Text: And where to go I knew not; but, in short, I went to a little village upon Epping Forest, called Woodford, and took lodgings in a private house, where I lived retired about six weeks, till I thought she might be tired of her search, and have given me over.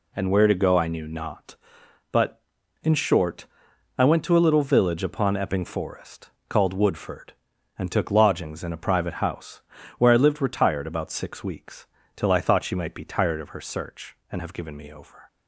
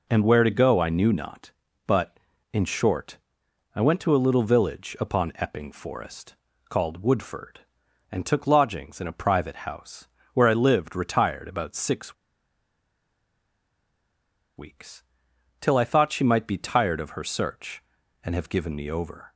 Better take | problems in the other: first | pauses between "six" and "weeks"; strong; at 12.1 s; 2.4 s long

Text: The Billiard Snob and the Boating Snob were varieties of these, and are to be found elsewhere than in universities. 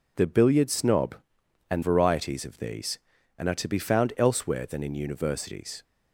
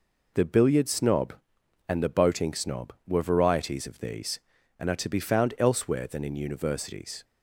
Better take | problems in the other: second | skips "the Boating Snob were"; at 1.8 s

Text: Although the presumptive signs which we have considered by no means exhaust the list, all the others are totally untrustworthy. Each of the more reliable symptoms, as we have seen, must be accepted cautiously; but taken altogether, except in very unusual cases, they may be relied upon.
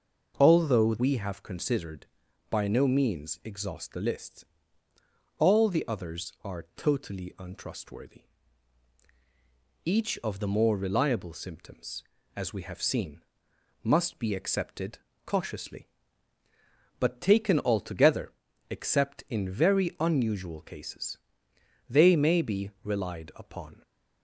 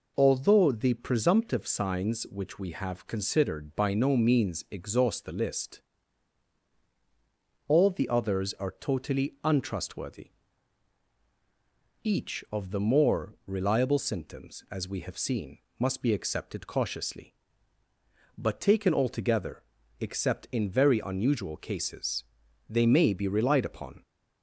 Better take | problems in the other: second | skips "the presumptive signs which"; at 0.9 s // pauses between "accepted" and "cautiously"; slight; at 14.9 s; 0.26 s long

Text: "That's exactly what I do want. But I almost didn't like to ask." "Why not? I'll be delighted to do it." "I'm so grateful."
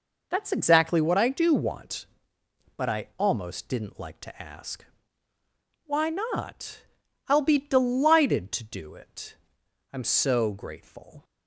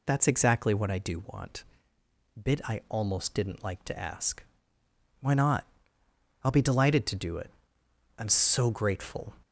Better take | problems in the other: first | says "Bit" for "But"; at 2.4 s

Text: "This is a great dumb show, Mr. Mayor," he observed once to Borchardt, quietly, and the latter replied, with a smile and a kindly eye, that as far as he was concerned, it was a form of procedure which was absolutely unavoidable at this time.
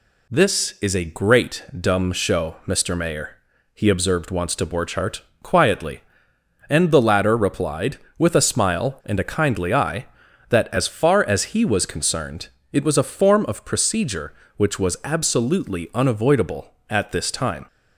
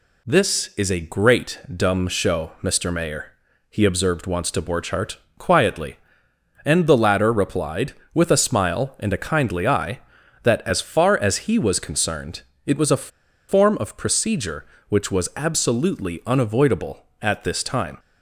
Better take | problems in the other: first | pauses between "a" and "form"; at 13.0 s; 0.41 s long

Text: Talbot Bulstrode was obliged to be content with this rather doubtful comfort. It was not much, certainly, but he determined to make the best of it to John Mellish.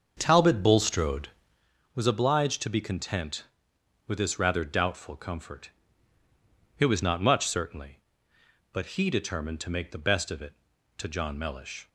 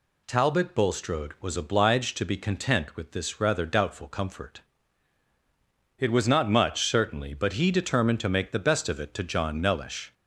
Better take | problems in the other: second | starts louder than the rest; until 1.7 s; 7 dB

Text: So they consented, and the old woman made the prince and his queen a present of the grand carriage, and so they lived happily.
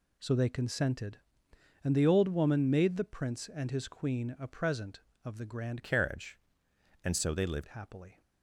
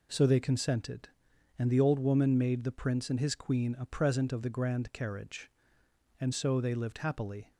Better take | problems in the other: second | changes voice from "carriage" to "lived"; from 5.8 to 7.6 s; 1.8 s long

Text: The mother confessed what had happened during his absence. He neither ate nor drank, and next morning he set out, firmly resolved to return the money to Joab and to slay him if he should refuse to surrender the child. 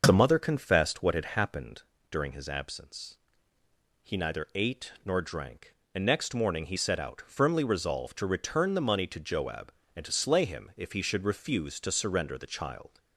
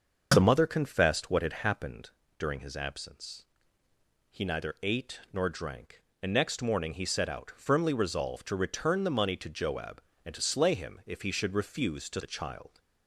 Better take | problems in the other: first | starts louder than the rest; noticeable; until 1.3 s; 6 dB; noticeable in the first // pauses between "happened" and "during"; slight; at 2.0 s; 0.30 s long; slight in the first // skips "surrender"; at 12.2 s

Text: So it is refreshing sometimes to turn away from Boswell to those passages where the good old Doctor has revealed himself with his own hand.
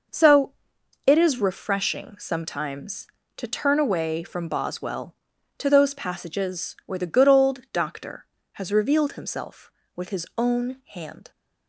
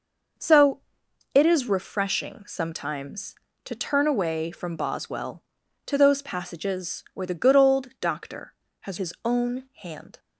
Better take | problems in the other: first | pauses between "So" and "it"; noticeable; at 0.7 s; 0.54 s long; noticeable in the first // skips "revealed himself with"; at 8.9 s

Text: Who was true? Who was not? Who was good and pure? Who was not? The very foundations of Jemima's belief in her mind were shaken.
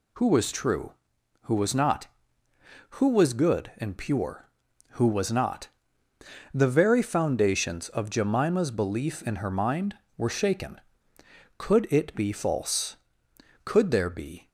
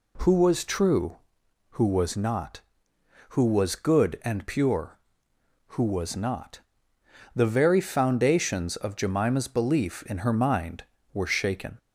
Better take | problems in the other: second | goes on to say "Could it be false Could there be"; strong; from 11.5 s on; 2.9 s long

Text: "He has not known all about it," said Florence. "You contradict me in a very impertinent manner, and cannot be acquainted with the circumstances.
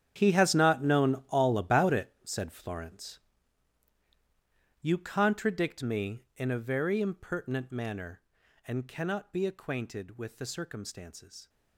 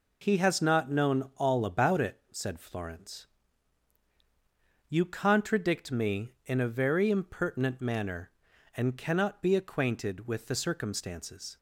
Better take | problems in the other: second | gets quieter; strong; throughout; 15 dB

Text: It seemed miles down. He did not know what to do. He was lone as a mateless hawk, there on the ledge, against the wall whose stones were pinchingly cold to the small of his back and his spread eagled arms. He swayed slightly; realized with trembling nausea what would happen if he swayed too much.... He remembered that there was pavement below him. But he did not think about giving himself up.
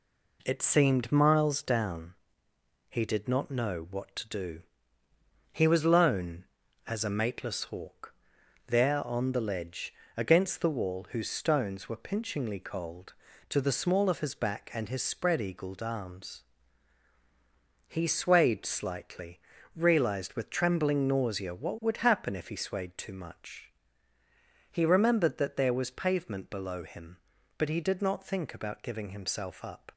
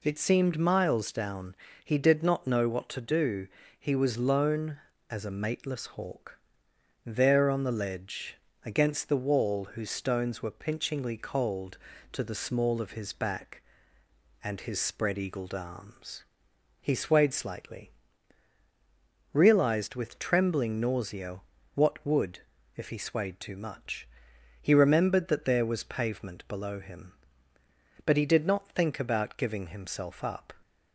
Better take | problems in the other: first | pauses between "nausea" and "what"; slight; at 21.4 s; 0.34 s long // skips "happen"; at 22.5 s

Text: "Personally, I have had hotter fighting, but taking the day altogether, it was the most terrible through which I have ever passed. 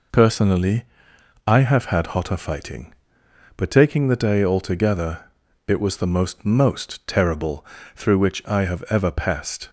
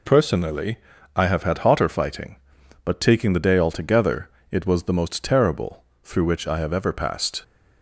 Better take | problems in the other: second | says "most" twice; at 6.4 s // pauses between "terrible" and "through"; slight; at 7.6 s; 0.30 s long; slight in the second

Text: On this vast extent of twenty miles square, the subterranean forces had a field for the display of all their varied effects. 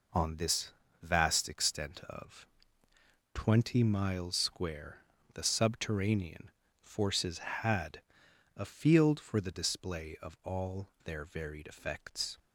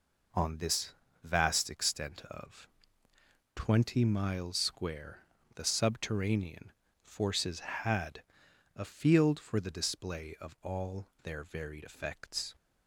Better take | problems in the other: neither | pauses between "this" and "vast"; slight; the same in both // pauses between "of" and "twenty"; noticeable; the same in both // pauses between "subterranean" and "forces"; slight; the same in both // pauses between "had" and "a"; noticeable; the same in both // pauses between "all" and "their"; slight; the same in both

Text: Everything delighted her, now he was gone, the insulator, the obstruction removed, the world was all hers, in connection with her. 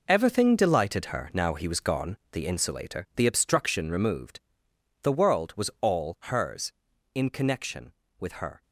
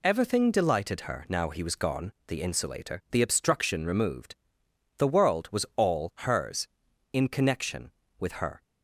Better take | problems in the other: second | gets quieter; strong; throughout; 11.5 dB

